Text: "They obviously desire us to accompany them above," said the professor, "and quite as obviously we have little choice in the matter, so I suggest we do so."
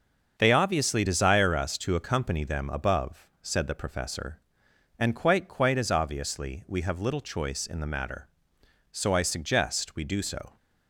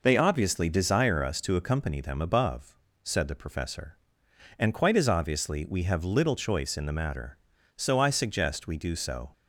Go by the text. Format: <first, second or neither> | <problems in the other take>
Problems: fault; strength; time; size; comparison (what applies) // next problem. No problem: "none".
second | starts louder than the rest; until 1.4 s; 6.5 dB // says "quite" twice; at 5.4 s